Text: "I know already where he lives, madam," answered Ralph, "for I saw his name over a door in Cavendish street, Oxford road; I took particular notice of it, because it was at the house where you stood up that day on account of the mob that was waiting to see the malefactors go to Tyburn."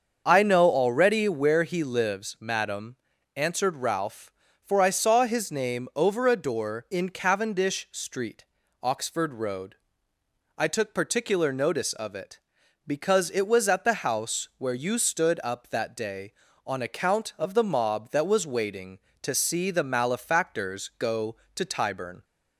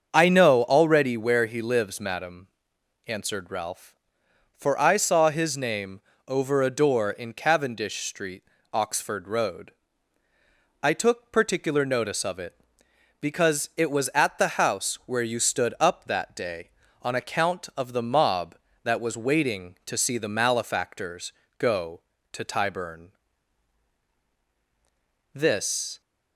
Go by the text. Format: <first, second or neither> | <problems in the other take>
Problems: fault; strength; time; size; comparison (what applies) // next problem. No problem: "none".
first | starts louder than the rest; until 1.1 s; 7 dB; also in the first // pauses between "name" and "over"; slight; at 6.0 s; 0.26 s long // pauses between "malefactors" and "go"; slight; at 21.3 s; 0.28 s long // goes on to say "This"; noticeable; from 25.3 s on; 0.68 s long